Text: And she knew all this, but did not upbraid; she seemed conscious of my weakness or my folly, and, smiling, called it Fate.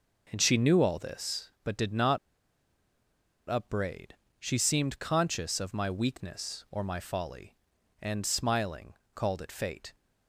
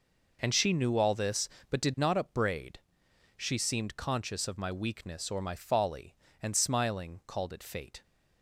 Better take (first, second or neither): second